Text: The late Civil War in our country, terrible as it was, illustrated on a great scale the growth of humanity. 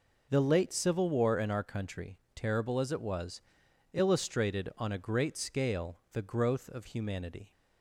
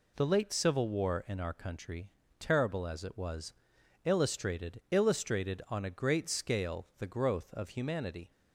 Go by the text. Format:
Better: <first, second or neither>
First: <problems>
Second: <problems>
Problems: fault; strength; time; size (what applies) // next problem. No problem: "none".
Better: first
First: none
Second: says "illustrated" twice; at 4.8 s